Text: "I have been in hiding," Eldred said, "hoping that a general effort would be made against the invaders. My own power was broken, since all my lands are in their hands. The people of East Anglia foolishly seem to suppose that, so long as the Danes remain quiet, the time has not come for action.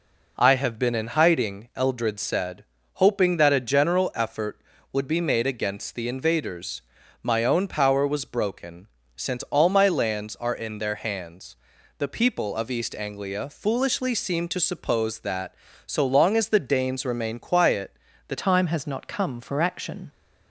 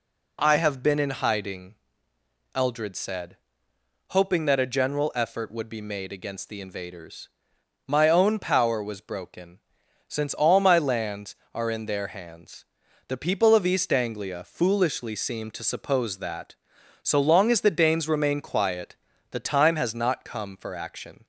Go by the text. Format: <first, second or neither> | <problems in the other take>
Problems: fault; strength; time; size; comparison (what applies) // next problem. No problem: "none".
second | changes voice at "time"; from 18.3 s on; 1.8 s long